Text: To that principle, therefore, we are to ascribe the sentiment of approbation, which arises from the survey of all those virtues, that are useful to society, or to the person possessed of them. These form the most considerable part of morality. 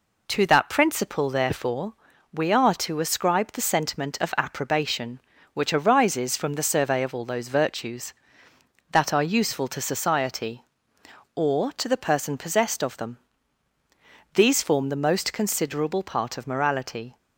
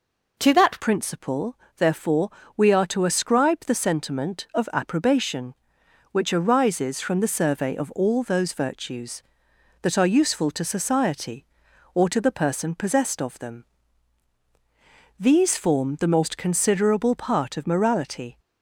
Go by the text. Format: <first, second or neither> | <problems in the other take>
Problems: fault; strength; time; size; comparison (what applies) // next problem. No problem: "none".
first | changes voice at "principle"; from 0.7 s on; 17.6 s long